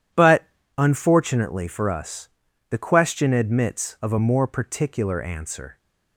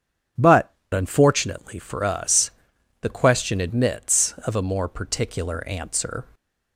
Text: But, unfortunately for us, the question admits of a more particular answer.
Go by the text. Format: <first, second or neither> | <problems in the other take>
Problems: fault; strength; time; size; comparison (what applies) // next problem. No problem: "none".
first | starts louder than the rest; strong; until 1.5 s; 8 dB // changes voice at "unfortunately"; from 0.9 s on; 5.3 s long